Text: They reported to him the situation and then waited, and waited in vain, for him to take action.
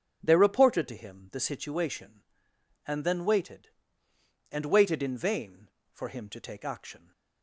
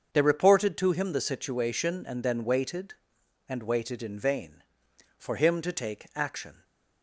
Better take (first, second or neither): neither